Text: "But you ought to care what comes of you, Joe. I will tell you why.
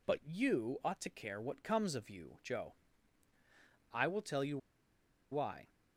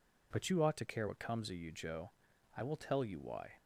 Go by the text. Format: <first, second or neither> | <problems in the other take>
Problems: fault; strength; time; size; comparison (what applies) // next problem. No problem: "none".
second | pauses between "you" and "why"; noticeable; at 4.5 s; 0.74 s long